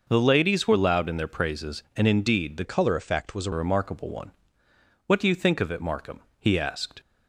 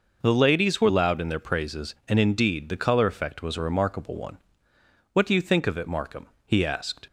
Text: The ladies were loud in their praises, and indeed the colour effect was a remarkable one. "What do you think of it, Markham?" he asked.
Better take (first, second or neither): second